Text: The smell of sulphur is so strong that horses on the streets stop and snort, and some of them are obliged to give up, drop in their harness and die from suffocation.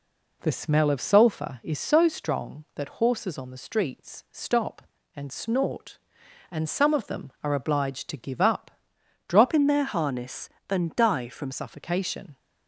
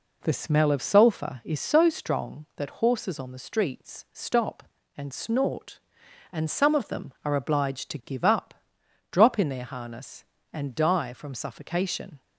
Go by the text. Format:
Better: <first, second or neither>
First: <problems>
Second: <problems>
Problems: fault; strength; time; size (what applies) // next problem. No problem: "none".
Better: second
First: changes voice from "in" to "from"; from 9.5 to 11.5 s; 2.0 s long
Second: none